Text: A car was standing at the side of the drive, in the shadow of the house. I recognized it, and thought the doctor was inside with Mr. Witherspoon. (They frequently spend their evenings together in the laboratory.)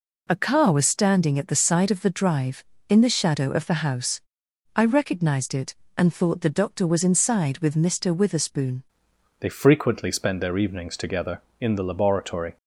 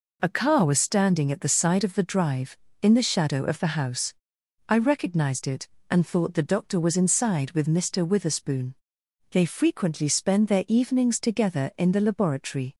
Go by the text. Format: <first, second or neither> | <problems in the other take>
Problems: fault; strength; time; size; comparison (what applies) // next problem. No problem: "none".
second | changes voice at "They"; from 9.3 s on; 3.2 s long